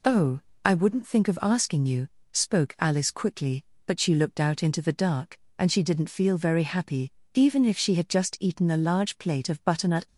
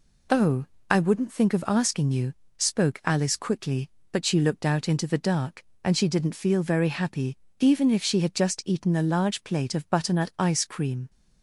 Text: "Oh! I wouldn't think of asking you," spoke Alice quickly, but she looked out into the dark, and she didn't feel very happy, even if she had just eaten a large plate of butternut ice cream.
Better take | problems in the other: second | stops before "ice cream"; at 10.0 s

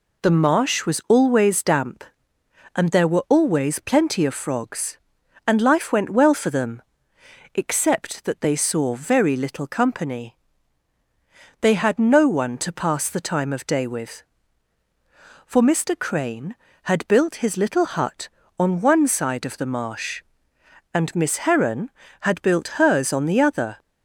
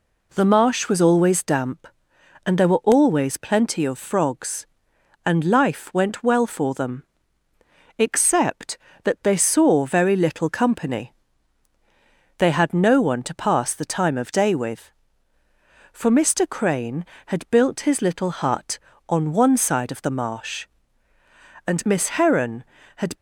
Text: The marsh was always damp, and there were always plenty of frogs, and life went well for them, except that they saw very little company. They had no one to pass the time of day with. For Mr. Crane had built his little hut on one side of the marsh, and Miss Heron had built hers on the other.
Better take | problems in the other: first | stops before "built hers on the other"; at 23.1 s

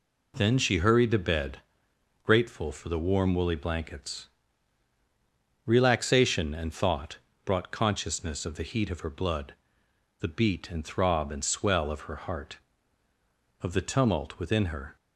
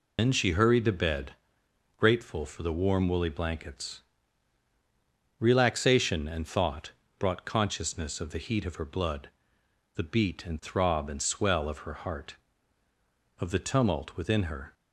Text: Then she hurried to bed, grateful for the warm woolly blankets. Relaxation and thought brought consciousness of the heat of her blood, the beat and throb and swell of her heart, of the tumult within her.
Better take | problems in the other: first | loses the start of "Then"; at 0.1 s; 110 ms // pauses between "thought" and "brought"; slight; at 6.9 s; 0.26 s long; slight in the first

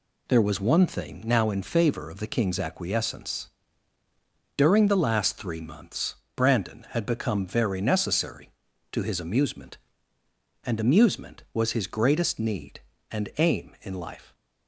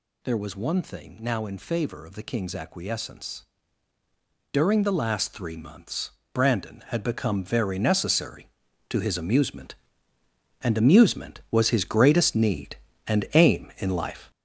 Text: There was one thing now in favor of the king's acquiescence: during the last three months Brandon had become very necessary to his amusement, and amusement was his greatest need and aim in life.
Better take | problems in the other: first | gets louder; throughout; 6.5 dB // pauses between "months" and "Brandon"; slight; at 6.1 s; 0.20 s long; slight in the first

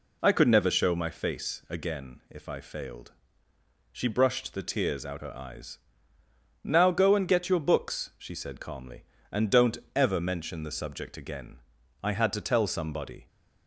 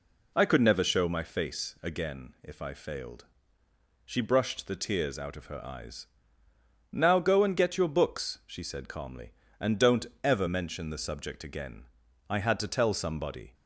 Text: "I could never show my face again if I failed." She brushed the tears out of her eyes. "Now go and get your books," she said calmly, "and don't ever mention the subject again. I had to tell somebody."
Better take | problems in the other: second | skips "of"; at 5.1 s // pauses between "don't" and "ever"; slight; at 9.7 s; 0.18 s long; slight in the second

